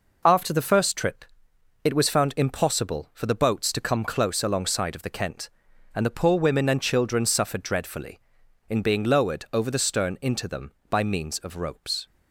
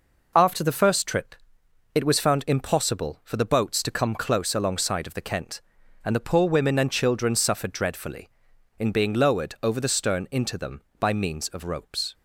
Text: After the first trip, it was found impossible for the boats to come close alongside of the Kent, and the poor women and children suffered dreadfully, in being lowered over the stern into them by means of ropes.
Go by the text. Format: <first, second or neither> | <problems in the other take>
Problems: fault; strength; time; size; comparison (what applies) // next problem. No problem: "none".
neither | none